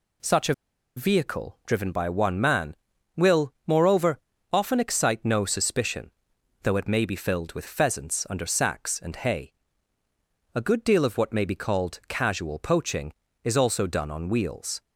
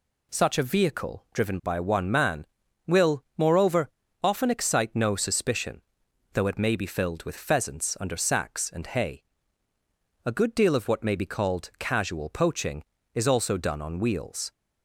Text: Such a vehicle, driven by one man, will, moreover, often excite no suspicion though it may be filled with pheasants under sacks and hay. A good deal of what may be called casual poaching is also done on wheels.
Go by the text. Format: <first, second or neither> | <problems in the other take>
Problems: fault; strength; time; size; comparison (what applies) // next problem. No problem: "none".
second | pauses between "a" and "vehicle"; at 0.5 s; 0.43 s long // pauses between "suspicion" and "though"; noticeable; at 6.1 s; 0.52 s long; noticeable in the second